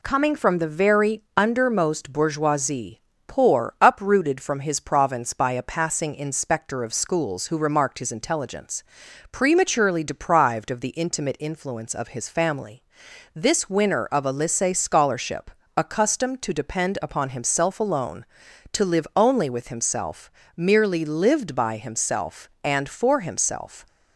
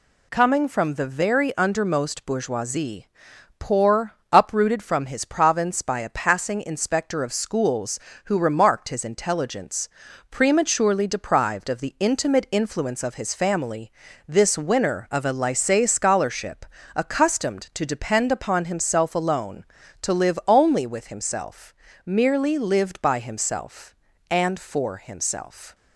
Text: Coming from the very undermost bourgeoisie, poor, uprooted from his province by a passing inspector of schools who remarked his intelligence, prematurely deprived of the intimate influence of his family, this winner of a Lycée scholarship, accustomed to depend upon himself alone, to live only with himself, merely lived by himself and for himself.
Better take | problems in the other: neither | none

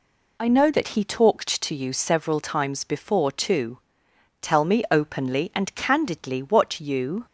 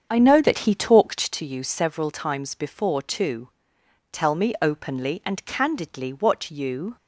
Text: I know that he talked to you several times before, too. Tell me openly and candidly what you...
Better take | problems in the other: first | starts louder than the rest; strong; until 1.3 s; 7.5 dB

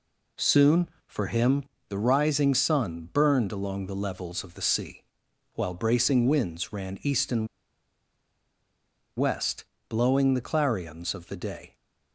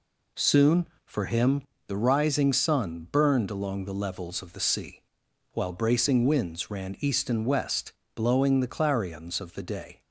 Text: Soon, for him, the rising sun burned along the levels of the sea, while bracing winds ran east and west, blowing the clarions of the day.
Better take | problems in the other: second | pauses between "and" and "west"; strong; at 7.4 s; 1.6 s long

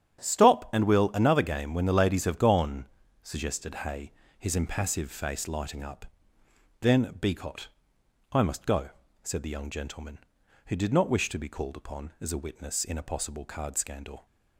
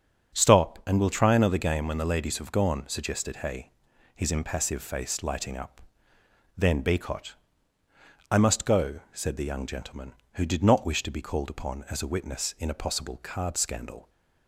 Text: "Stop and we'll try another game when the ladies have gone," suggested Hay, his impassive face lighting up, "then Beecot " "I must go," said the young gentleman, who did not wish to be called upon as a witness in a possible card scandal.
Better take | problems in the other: second | starts louder than the rest; strong; until 1.3 s; 10.5 dB; strong in the second // skips "try"; at 1.1 s

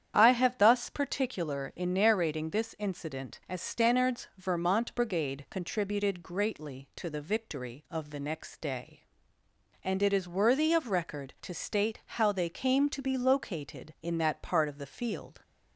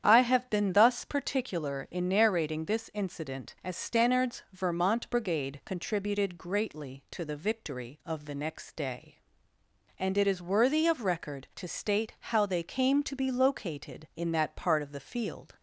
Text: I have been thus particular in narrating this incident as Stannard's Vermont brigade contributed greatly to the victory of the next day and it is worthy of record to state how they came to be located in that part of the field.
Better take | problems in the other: second | starts louder than the rest; strong; until 1.2 s; 9 dB; strong in the second // skips "been"; at 0.5 s

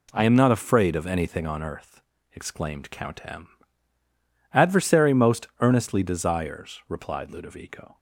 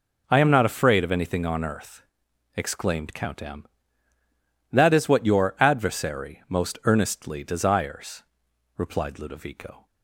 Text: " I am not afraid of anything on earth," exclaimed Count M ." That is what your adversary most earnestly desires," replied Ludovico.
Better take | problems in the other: second | skips "That is what your"; at 4.5 s

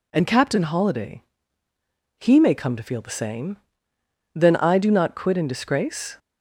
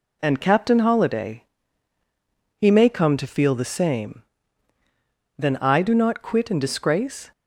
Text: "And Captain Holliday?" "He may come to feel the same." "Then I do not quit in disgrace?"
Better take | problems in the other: neither | none

